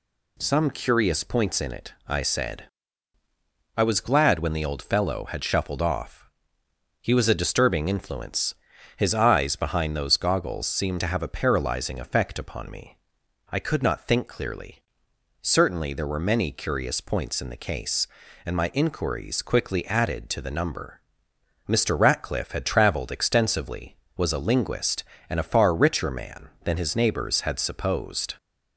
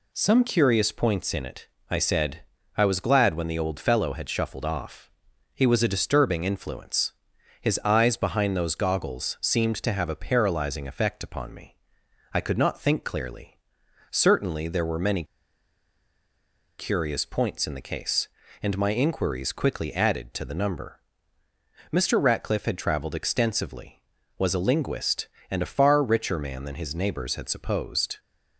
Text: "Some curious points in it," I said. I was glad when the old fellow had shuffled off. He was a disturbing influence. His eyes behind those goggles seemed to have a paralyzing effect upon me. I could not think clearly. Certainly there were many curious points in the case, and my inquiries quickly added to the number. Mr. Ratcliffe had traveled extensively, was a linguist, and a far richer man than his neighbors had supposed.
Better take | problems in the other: first | pauses between "many" and "curious"; strong; at 15.2 s; 1.5 s long

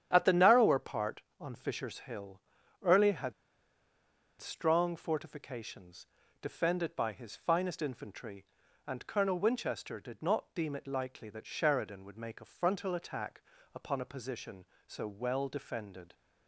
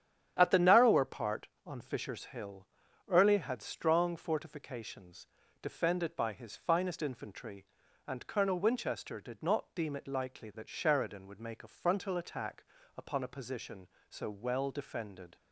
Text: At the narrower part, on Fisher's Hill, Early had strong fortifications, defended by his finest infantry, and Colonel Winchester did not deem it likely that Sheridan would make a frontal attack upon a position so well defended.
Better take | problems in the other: second | starts louder than the rest; strong; until 1.1 s; 9.5 dB; strong in the second // pauses between "had" and "strong"; at 3.3 s; 1.0 s long // pauses between "attack" and "upon"; slight; at 13.4 s; 0.32 s long; slight in the second

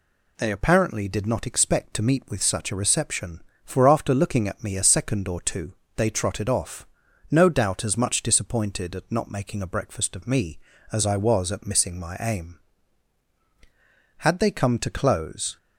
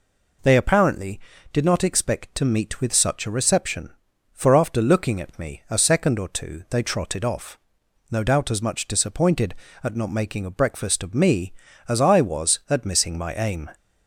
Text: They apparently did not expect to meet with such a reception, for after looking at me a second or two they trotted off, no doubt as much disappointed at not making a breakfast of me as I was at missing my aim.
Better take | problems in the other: second | pauses between "two" and "they"; slight; at 5.7 s; 0.22 s long // goes on to say "Had they come to close"; from 14.1 s on; 1.3 s long

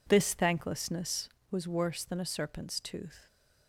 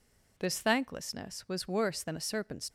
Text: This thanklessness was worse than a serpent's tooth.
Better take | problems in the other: first | stops before "tooth"; at 2.6 s

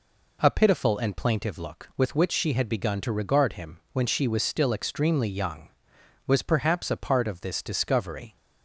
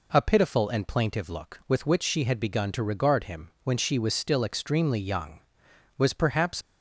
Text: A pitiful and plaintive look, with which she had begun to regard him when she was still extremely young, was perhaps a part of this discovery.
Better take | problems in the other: first | stops before "a part of this discovery"; at 6.6 s

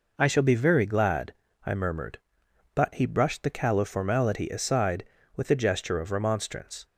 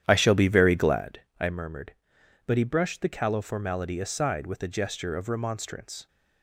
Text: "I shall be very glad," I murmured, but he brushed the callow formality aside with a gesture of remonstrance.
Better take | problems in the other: first | starts louder than the rest; strong; until 1.1 s; 10.5 dB

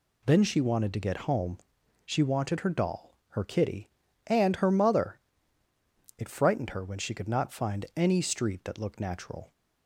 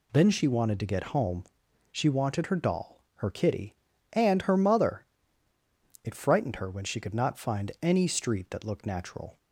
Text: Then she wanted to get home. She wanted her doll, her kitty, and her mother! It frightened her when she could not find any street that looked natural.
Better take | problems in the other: neither | none

